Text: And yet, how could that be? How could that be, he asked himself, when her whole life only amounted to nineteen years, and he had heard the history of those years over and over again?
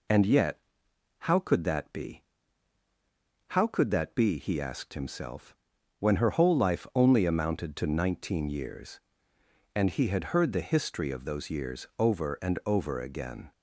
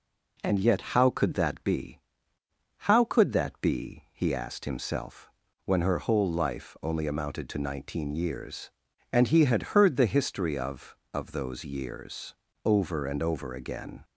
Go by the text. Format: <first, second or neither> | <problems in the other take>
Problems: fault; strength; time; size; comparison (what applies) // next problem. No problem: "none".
first | says "of" twice; at 11.1 s // pauses between "years" and "over"; slight; at 12.3 s; 0.30 s long